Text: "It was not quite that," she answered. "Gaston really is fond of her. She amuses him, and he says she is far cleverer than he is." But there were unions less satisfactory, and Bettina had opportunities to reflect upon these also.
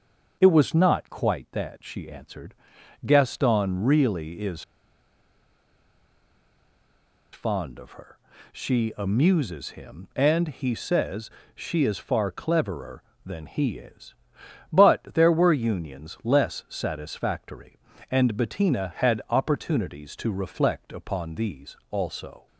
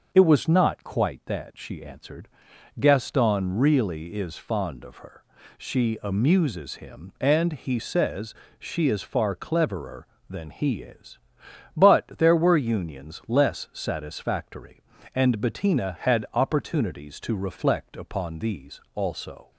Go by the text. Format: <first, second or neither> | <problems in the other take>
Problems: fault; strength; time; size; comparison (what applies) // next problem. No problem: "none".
second | starts louder than the rest; until 1.4 s; 6.5 dB; also in the second // pauses between "is" and "fond"; strong; at 4.6 s; 2.7 s long // pauses between "says" and "she"; slight; at 11.3 s; 0.24 s long; slight in the second